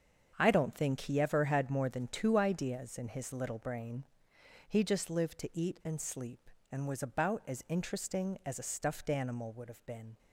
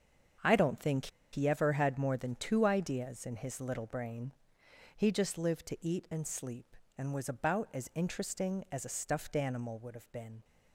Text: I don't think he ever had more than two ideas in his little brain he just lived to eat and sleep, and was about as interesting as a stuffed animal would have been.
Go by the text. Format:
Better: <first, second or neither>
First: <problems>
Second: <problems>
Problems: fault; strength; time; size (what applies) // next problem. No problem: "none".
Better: first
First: starts louder than the rest; strong; until 1.3 s; 7.5 dB // pauses between "brain" and "he"; noticeable; at 4.0 s; 0.62 s long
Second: starts louder than the rest; strong; until 1.6 s; 7.5 dB // pauses between "think" and "he"; slight; at 1.0 s; 0.25 s long // pauses between "brain" and "he"; noticeable; at 4.3 s; 0.62 s long